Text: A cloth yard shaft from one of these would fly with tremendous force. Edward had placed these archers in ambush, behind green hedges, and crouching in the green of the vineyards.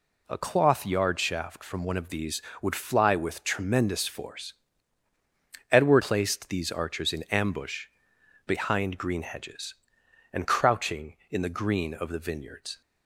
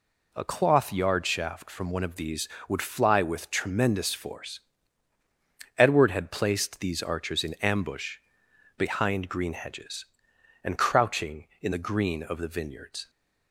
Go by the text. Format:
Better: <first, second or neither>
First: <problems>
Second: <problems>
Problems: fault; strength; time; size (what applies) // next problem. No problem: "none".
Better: second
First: skips "had"; at 6.0 s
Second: none